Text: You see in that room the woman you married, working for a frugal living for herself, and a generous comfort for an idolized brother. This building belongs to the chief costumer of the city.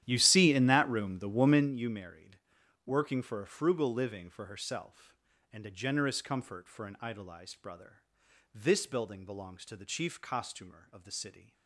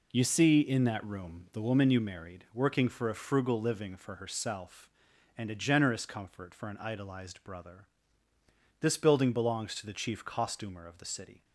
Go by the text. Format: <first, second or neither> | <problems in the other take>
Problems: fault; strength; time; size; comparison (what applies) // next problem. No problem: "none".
second | starts louder than the rest; strong; until 1.8 s; 11.5 dB